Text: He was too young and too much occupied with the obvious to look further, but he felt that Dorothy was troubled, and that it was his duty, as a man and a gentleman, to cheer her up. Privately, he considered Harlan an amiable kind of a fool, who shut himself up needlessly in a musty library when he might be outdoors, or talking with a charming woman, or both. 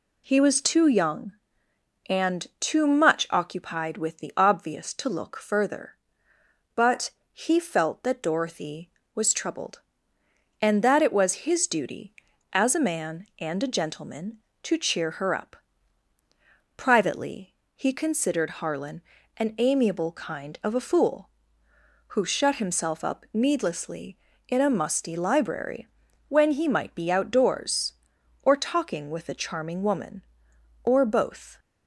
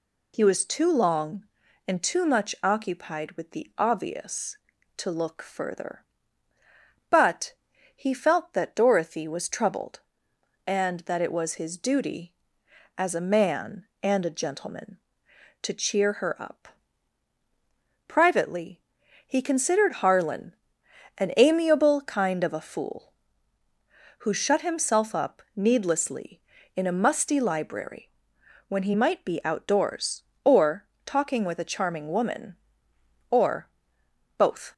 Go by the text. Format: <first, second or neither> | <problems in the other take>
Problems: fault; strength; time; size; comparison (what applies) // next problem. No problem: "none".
first | says "long" for "young"; at 0.9 s // pauses between "but" and "he"; at 7.5 s; 0.42 s long; slight in the first // pauses between "Harlan" and "an"; noticeable; at 20.5 s; 0.64 s long; slight in the first // pauses between "library" and "when"; noticeable; at 28.1 s; 0.58 s long; also in the first // pauses between "or" and "talking"; slight; at 30.8 s; 0.20 s long // pauses between "or" and "both"; noticeable; at 33.6 s; 0.68 s long